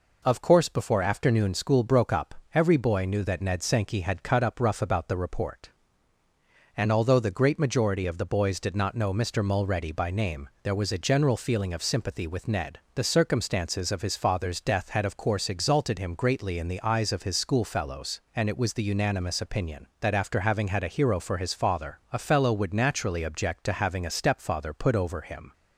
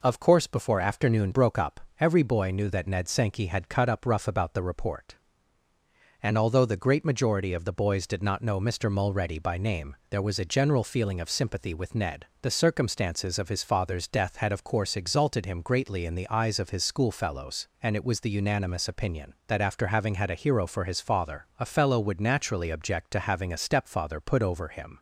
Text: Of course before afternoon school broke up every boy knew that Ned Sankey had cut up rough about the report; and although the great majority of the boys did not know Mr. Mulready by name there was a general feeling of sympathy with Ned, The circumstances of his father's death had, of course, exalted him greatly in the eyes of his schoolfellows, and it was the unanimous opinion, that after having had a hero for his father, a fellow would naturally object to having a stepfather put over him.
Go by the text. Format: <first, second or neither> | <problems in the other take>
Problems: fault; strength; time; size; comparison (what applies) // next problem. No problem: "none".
first | skips "school"; at 1.3 s // pauses between "up" and "every"; slight; at 1.7 s; 0.20 s long; slight in the first